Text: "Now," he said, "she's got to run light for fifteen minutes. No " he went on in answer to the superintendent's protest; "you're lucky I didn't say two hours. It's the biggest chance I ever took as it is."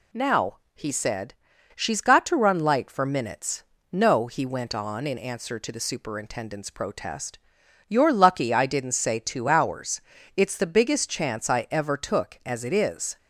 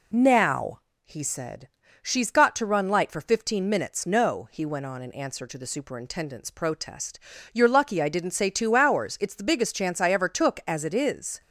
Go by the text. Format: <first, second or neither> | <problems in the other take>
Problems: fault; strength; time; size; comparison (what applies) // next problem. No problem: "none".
second | skips "fifteen"; at 3.0 s